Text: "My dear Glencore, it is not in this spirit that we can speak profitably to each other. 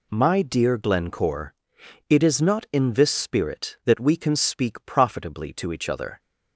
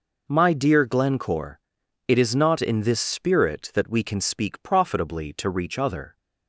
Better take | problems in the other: first | says "reach" for "each"; at 5.4 s

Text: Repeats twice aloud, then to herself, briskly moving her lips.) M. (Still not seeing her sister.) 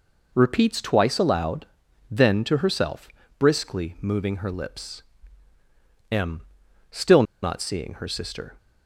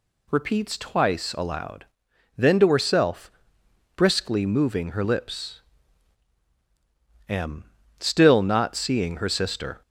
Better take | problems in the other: second | pauses between "Still" and "not"; slight; at 7.2 s; 0.18 s long

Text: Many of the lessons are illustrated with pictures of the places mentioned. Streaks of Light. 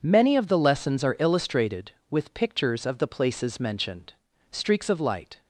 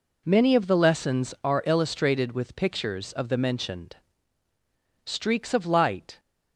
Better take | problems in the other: first | skips "places"; at 3.3 s

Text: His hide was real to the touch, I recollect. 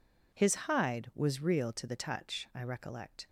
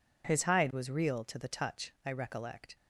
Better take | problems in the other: neither | none

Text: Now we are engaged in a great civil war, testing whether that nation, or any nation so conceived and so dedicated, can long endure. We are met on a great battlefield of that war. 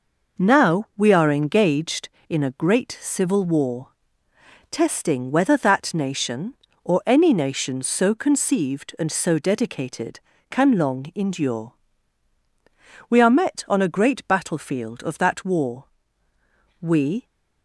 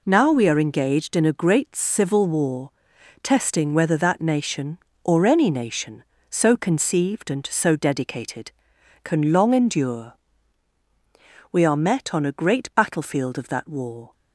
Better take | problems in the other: second | goes on to say "We"; slight; from 16.8 s on; 0.44 s long

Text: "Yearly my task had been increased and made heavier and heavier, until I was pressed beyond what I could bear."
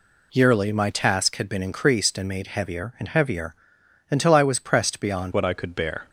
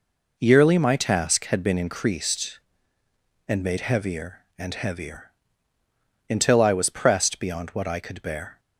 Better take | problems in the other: second | changes voice at "what"; from 5.3 s on; 0.7 s long

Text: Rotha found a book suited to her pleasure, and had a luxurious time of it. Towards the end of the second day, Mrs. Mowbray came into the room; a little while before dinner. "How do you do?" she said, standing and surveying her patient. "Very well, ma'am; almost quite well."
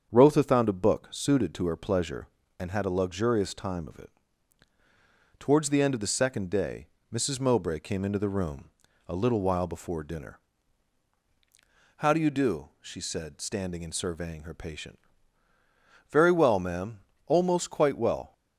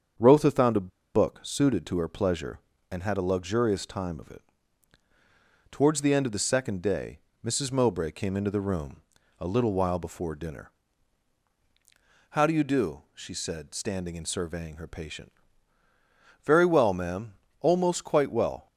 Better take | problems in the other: first | starts louder than the rest; strong; until 1.4 s; 7.5 dB; strong in the first // pauses between "a" and "book"; slight; at 0.9 s; 0.24 s long

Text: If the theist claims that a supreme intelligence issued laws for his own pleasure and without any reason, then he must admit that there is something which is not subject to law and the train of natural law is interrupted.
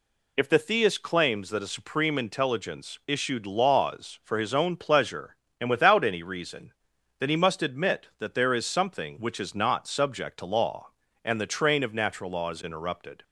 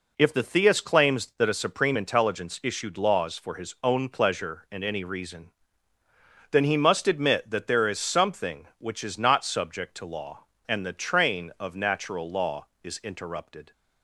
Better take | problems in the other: first | skips "without"; at 4.8 s

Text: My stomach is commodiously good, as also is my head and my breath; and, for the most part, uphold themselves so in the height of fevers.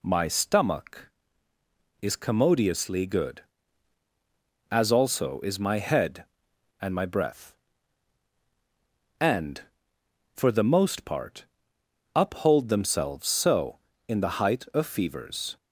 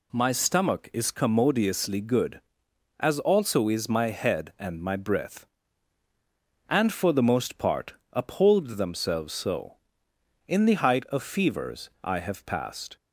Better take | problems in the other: first | goes on to say "I have passed"; noticeable; from 12.0 s on; 0.94 s long

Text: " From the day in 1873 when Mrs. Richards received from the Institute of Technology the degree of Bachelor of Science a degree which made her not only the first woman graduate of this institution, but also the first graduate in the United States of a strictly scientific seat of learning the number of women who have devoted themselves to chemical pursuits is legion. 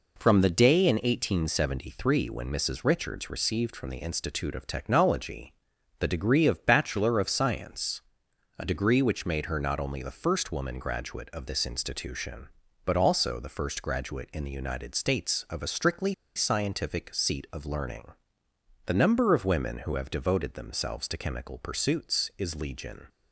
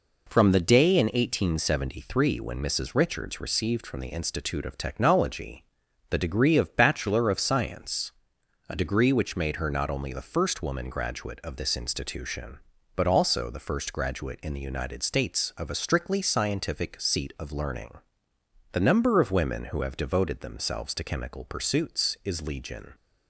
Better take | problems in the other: second | pauses between "Technology" and "the"; noticeable; at 5.5 s; 0.46 s long; noticeable in the second // pauses between "Science" and "a"; noticeable; at 8.0 s; 0.56 s long; noticeable in the second // pauses between "strictly" and "scientific"; slight; at 16.1 s; 0.21 s long // pauses between "learning" and "the"; noticeable; at 18.1 s; 0.74 s long; noticeable in the second

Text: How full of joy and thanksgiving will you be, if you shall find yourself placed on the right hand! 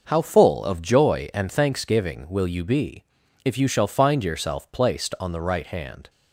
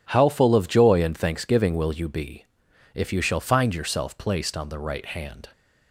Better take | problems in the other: neither | none

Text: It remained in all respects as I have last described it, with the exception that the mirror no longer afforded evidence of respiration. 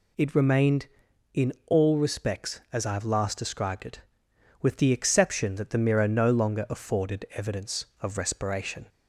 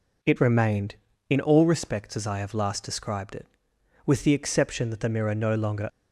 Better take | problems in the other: first | stops before "afforded evidence of respiration"; at 5.8 s

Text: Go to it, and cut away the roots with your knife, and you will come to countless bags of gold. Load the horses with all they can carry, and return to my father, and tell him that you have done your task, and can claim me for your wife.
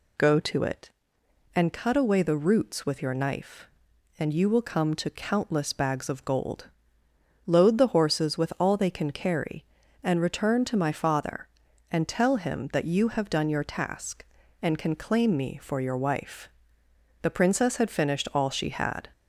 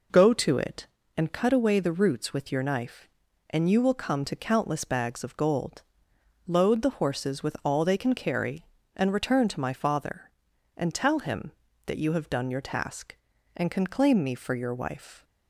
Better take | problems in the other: second | goes on to say "The princess had finished all she had"; strong; from 17.2 s on; 1.8 s long

